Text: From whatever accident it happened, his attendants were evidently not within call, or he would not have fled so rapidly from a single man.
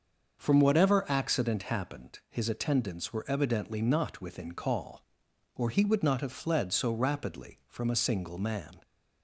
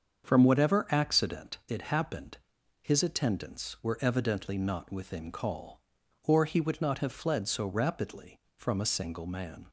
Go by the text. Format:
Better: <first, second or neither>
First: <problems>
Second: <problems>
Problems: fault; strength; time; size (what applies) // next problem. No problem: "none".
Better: second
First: starts louder than the rest; until 1.4 s; 6.5 dB // skips "it"; at 1.6 s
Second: starts louder than the rest; until 1.2 s; 7 dB